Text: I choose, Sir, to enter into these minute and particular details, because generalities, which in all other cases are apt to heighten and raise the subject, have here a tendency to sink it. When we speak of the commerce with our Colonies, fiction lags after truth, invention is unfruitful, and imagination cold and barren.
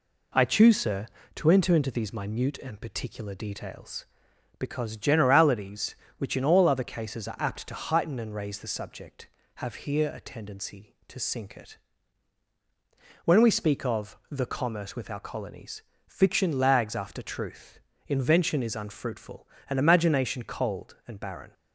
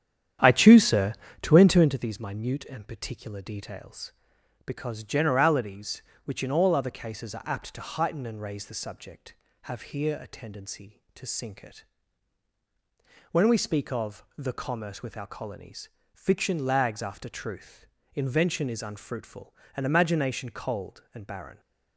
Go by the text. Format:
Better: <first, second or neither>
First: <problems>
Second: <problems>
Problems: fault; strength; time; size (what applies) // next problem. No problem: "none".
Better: first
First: none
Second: starts louder than the rest; strong; until 2.1 s; 9.5 dB